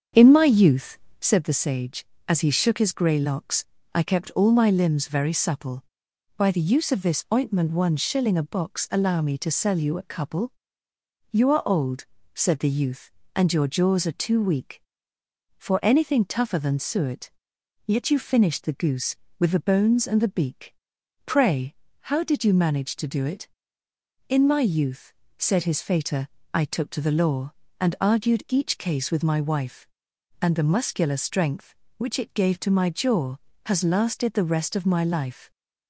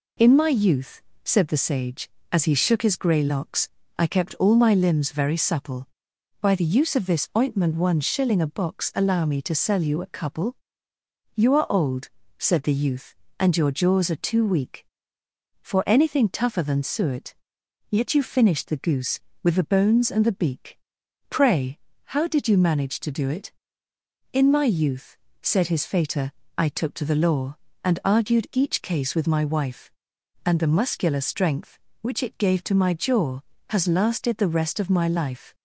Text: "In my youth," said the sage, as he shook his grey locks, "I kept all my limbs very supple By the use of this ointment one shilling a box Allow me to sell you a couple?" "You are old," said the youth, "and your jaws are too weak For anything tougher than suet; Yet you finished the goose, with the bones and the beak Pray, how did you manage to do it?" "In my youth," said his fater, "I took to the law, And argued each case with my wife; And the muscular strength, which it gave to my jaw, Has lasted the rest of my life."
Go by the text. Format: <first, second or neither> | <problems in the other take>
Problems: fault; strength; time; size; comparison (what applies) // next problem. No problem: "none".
second | starts louder than the rest; strong; until 1.3 s; 7.5 dB // pauses between "beak" and "Pray"; noticeable; at 20.7 s; 0.50 s long; noticeable in the second